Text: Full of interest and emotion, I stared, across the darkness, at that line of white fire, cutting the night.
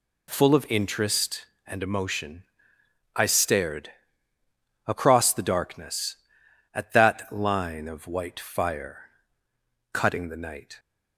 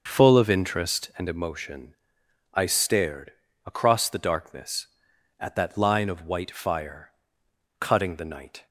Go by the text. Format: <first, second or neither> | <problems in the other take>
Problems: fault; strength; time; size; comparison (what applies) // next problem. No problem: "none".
first | starts louder than the rest; noticeable; until 1.3 s; 6 dB